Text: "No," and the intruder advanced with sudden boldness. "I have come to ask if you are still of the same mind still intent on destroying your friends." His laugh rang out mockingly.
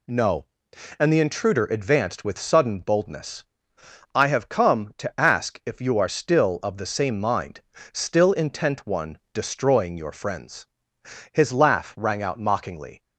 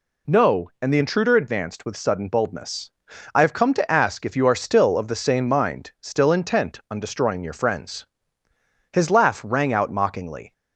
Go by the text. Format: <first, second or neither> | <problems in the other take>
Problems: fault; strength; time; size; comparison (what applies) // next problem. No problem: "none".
second | pauses between "mind" and "still"; slight; at 7.5 s; 0.32 s long // says "one" for "on"; at 8.8 s